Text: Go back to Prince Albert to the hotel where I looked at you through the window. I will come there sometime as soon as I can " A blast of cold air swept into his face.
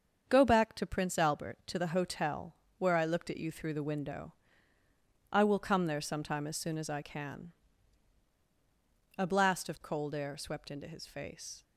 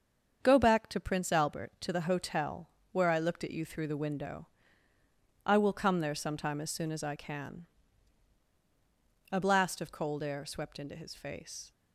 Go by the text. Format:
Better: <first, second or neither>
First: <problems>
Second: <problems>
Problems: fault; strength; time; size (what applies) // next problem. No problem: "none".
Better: neither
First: starts louder than the rest; until 1.2 s; 7 dB // pauses between "hotel" and "where"; slight; at 2.5 s; 0.22 s long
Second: starts louder than the rest; until 1.4 s; 7 dB // pauses between "hotel" and "where"; slight; at 2.6 s; 0.22 s long